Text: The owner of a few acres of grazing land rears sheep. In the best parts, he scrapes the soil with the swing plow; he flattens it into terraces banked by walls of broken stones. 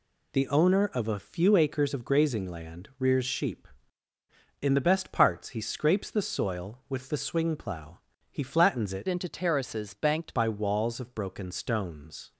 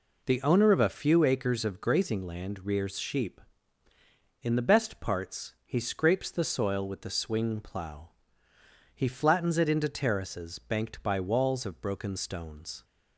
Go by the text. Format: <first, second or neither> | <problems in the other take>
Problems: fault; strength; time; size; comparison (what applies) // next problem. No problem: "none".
second | changes voice from "into" to "banked"; from 9.0 to 10.3 s; 1.3 s long